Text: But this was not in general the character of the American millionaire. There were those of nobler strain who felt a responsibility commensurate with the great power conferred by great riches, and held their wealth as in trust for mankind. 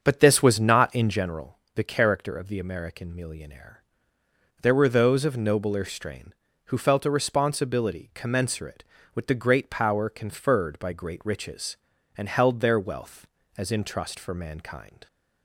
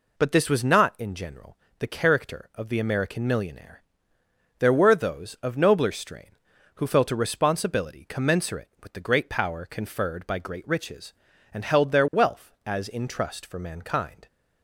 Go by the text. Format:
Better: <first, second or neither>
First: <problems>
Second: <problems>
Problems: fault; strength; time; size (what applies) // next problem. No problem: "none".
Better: second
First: starts louder than the rest; until 1.2 s; 7 dB // pauses between "general" and "the"; slight; at 1.5 s; 0.16 s long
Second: pauses between "general" and "the"; slight; at 1.5 s; 0.22 s long